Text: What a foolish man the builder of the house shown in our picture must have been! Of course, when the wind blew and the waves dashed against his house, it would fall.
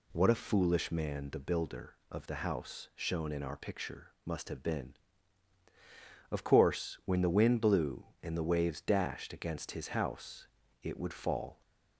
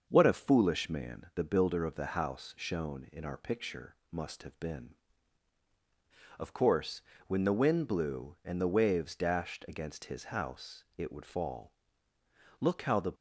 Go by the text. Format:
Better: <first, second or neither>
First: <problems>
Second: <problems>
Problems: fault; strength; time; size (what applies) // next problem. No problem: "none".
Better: first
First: none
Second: starts louder than the rest; until 1.1 s; 6.5 dB // goes on to say "Look how the"; from 12.6 s on; 0.52 s long